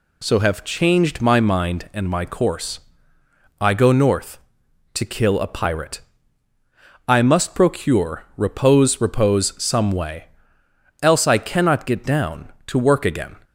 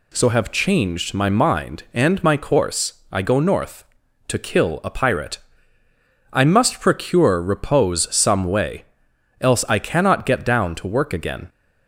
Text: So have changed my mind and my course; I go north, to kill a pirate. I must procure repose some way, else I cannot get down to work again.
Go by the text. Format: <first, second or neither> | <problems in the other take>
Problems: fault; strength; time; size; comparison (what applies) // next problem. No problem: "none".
second | says "repose" twice; at 9.0 s